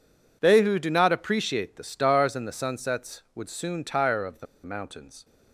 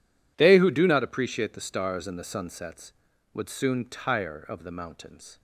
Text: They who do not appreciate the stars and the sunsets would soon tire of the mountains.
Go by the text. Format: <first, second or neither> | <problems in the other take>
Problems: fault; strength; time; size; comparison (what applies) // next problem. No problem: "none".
second | pauses between "the" and "mountains"; slight; at 4.4 s; 0.19 s long